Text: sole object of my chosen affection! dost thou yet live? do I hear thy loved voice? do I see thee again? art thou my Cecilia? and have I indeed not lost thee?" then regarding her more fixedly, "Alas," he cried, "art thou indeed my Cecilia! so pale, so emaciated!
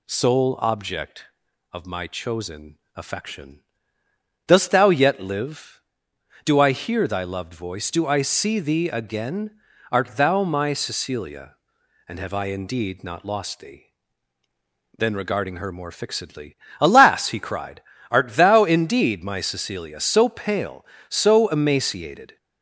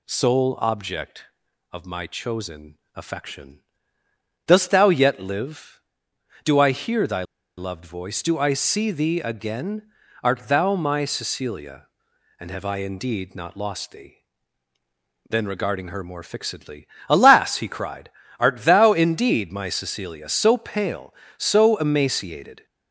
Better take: first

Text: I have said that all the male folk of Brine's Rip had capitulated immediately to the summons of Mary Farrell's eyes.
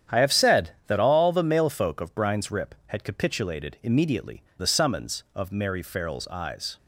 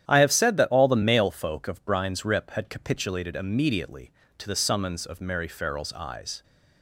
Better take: second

